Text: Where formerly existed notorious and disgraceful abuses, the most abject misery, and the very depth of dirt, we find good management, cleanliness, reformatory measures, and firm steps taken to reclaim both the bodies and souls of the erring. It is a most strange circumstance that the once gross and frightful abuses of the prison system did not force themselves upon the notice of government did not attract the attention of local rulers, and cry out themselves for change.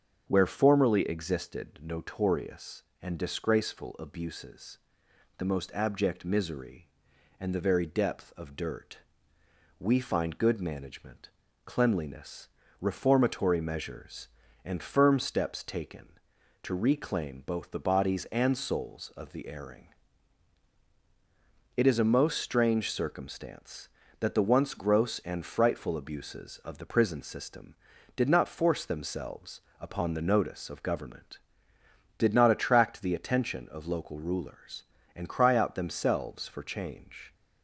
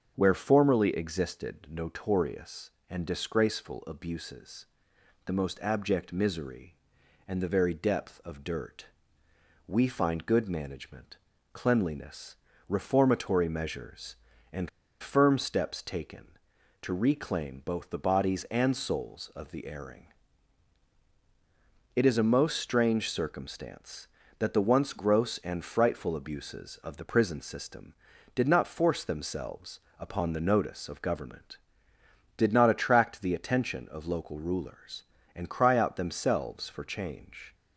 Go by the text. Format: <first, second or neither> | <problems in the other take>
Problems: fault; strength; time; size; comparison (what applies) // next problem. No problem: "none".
first | starts louder than the rest; until 1.1 s; 7 dB; also in the first // pauses between "and" and "firm"; slight; at 14.6 s; 0.33 s long // pauses between "themselves" and "upon"; slight; at 29.8 s; 0.18 s long; slight in the first